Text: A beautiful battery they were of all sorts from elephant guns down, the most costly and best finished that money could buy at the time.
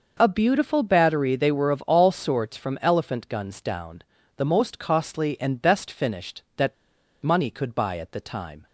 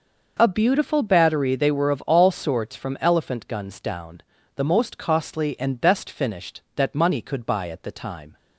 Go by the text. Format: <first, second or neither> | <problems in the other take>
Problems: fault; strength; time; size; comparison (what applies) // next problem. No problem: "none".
second | pauses between "that" and "money"; noticeable; at 6.7 s; 0.48 s long